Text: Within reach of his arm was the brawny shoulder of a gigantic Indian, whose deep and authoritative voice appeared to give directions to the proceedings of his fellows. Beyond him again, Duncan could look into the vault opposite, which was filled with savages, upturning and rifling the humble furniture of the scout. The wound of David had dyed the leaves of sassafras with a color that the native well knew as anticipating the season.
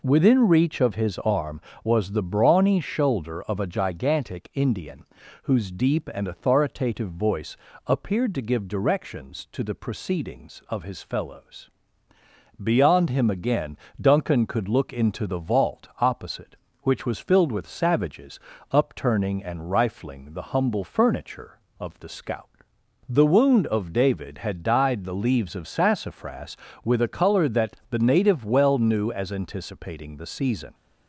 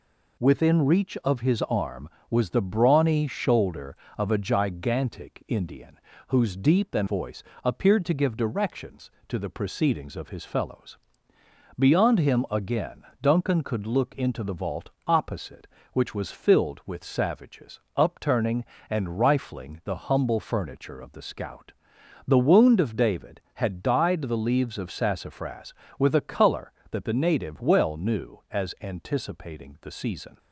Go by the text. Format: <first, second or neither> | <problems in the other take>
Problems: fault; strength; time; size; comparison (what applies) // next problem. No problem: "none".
first | skips "authoritative"; at 7.0 s // pauses between "voice" and "appeared"; slight; at 7.4 s; 0.20 s long; slight in the first // pauses between "vault" and "opposite"; slight; at 14.8 s; 0.16 s long